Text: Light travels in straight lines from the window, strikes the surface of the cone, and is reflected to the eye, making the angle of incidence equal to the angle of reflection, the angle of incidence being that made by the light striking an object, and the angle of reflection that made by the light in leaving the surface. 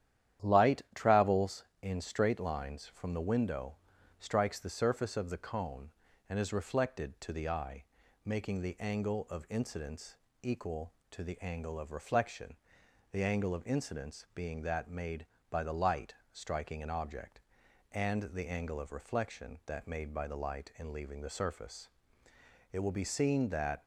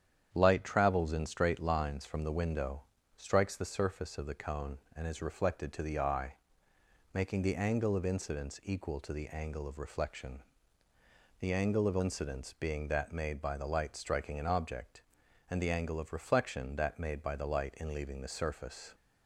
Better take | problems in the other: second | starts louder than the rest; strong; until 1.5 s; 10.5 dB; strong in the second // pauses between "incidence" and "equal"; slight; at 10.1 s; 0.24 s long // pauses between "light" and "striking"; slight; at 16.1 s; 0.18 s long // goes on to say "It will be seen that"; noticeable; from 22.7 s on; 1.1 s long

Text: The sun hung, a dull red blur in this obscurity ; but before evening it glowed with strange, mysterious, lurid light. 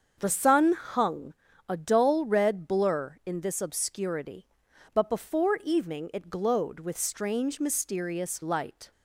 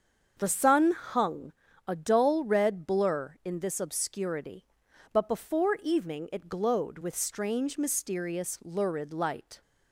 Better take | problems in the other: second | starts louder than the rest; until 1.1 s; 7 dB; also in the second // skips "lurid"; at 8.4 s

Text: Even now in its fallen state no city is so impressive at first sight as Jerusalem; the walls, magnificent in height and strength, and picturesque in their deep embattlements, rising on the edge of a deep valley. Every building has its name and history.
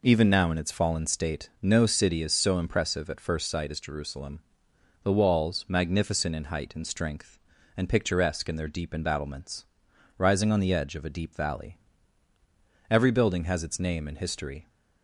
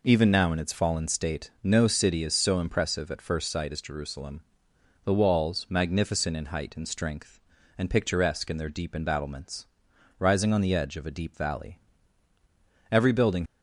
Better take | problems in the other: first | stops before "has its name and history"; at 13.4 s

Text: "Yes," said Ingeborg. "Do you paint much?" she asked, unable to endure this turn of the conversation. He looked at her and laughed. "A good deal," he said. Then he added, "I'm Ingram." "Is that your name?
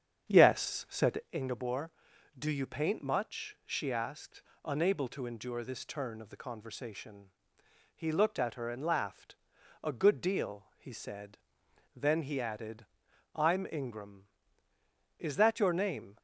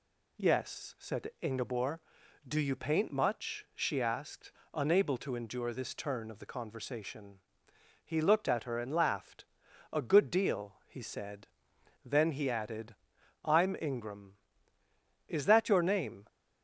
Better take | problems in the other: second | starts louder than the rest; strong; until 1.3 s; 8 dB

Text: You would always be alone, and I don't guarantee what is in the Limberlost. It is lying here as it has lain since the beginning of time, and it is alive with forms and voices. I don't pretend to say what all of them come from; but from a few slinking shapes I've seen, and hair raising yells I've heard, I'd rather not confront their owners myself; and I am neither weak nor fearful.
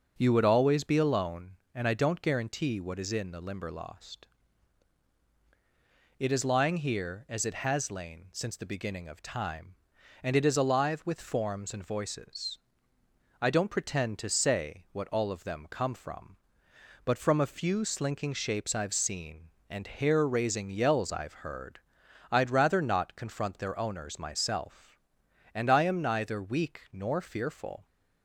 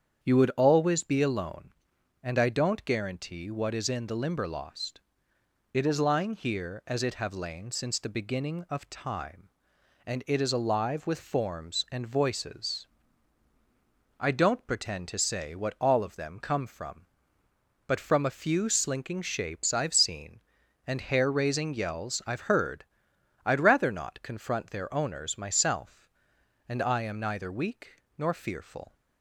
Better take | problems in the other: first | starts louder than the rest; strong; until 1.2 s; 8 dB // says "have" for "has"; at 7.1 s // pauses between "weak" and "nor"; slight; at 28.0 s; 0.16 s long

